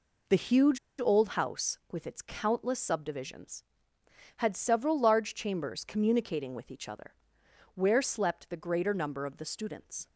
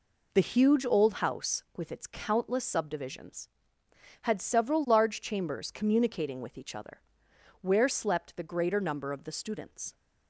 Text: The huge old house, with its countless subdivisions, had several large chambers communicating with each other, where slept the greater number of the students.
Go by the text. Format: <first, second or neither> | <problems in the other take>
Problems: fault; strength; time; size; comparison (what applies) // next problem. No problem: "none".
second | pauses between "huge" and "old"; slight; at 0.7 s; 0.20 s long